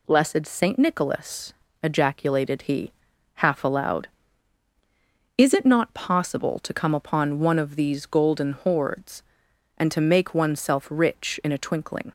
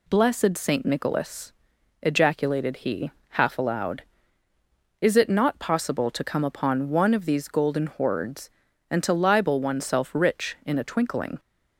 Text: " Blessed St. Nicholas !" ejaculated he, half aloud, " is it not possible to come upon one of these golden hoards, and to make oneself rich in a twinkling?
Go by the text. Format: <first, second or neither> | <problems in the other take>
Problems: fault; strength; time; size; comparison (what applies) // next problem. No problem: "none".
first | says "libel" for "make"; at 9.1 s